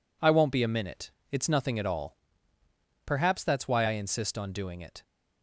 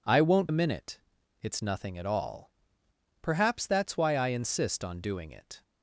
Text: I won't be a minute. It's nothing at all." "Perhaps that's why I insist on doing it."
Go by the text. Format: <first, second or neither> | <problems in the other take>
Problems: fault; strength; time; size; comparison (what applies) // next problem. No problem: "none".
first | skips "be"; at 0.4 s